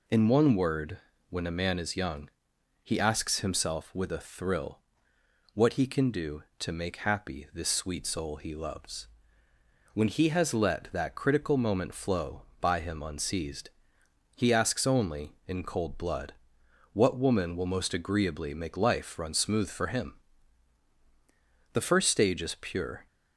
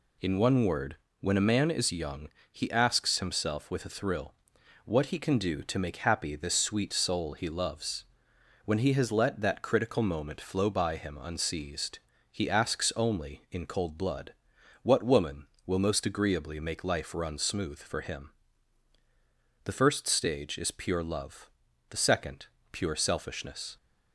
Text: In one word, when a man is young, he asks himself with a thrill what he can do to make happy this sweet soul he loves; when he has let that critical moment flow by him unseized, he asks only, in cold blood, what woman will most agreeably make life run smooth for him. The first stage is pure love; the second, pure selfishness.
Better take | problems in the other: second | pauses between "thrill" and "what"; noticeable; at 4.7 s; 0.76 s long; noticeable in the second // stops before "love the second pure selfishness"; at 23.0 s

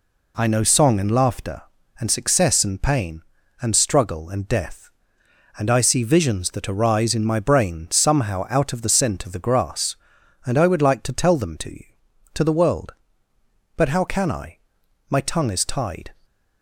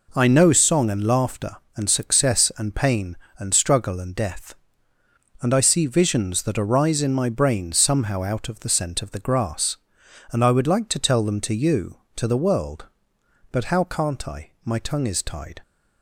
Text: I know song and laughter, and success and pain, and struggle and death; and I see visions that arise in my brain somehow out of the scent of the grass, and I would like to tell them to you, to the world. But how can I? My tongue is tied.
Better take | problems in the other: first | says "can't" for "can"; at 13.8 s

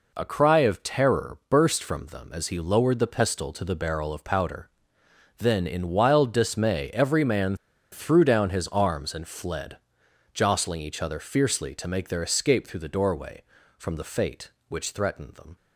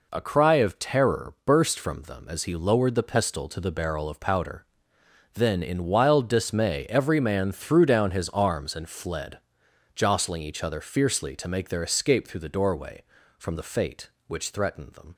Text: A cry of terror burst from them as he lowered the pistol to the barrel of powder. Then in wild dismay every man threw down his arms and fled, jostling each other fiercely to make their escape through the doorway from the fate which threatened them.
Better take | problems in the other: second | pauses between "man" and "threw"; at 7.5 s; 0.37 s long

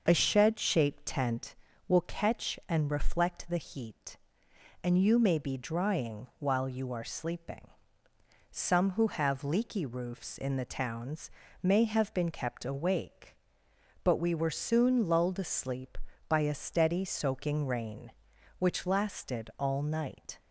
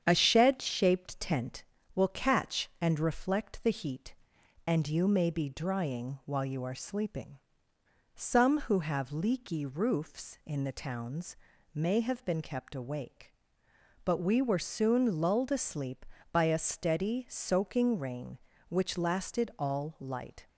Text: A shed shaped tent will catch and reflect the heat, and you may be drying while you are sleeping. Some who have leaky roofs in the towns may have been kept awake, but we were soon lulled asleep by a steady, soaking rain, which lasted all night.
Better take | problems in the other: first | starts louder than the rest; strong; until 1.0 s; 8.5 dB; noticeable in the first // pauses between "towns" and "may"; slight; at 11.3 s; 0.36 s long; slight in the first // says "light" for "night"; at 19.9 s

